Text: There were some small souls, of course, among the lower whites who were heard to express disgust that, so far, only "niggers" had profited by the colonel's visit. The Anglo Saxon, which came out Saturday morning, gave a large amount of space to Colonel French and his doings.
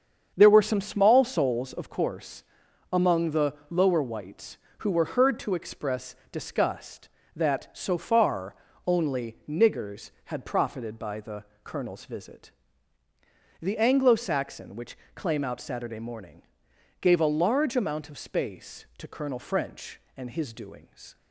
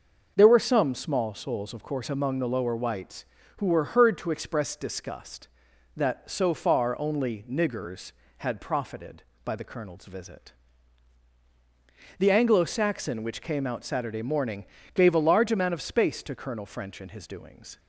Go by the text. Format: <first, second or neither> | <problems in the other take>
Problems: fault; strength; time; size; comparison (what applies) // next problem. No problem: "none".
second | starts louder than the rest; strong; until 1.3 s; 7.5 dB // pauses between "the" and "lower"; slight; at 3.5 s; 0.16 s long // pauses between "express" and "disgust"; slight; at 6.1 s; 0.16 s long // pauses between "the" and "colonel's"; slight; at 11.4 s; 0.18 s long // says "claim" for "came"; at 15.1 s